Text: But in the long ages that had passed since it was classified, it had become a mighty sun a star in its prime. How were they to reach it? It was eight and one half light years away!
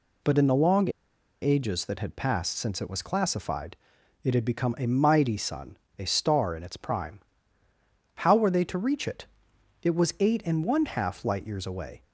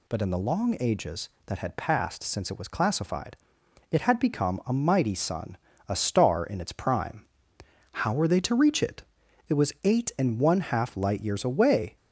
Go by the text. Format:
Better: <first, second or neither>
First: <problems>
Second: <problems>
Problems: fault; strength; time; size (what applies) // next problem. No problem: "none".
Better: second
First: pauses between "long" and "ages"; noticeable; at 0.8 s; 0.52 s long // pauses between "sun" and "a"; slight; at 5.7 s; 0.22 s long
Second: pauses between "sun" and "a"; slight; at 5.5 s; 0.28 s long